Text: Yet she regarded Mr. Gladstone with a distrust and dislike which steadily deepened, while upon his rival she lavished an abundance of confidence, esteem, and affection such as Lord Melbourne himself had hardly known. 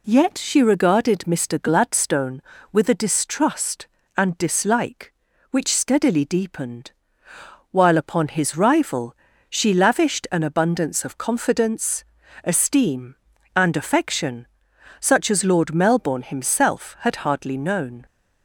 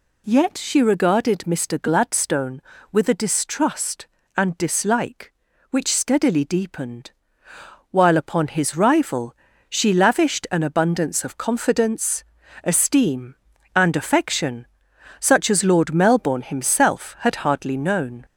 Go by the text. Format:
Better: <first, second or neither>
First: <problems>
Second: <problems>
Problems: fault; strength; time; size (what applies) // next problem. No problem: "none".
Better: first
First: pauses between "rival" and "she"; slight; at 9.1 s; 0.32 s long // pauses between "affection" and "such"; noticeable; at 14.4 s; 0.54 s long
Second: gets louder; slight; throughout; 3 dB // pauses between "rival" and "she"; slight; at 9.3 s; 0.32 s long // pauses between "affection" and "such"; noticeable; at 14.6 s; 0.54 s long